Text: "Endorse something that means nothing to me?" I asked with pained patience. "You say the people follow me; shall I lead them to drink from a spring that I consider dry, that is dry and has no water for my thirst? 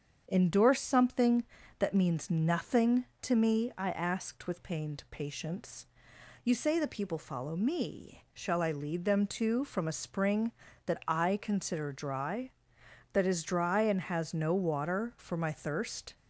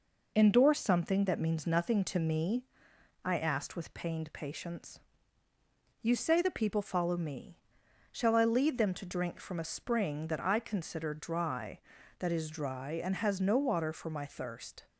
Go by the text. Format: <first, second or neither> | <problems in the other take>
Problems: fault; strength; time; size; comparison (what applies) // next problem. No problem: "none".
second | starts louder than the rest; strong; until 1.3 s; 7.5 dB // skips "drink"; at 9.6 s